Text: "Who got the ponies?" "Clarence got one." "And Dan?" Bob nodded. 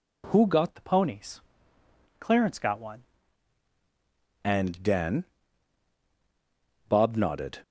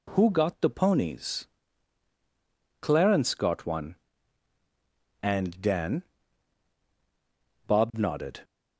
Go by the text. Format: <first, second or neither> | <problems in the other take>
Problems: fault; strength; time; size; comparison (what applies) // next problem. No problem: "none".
second | changes voice from "the" to "one"; from 0.7 to 3.0 s; 2.3 s long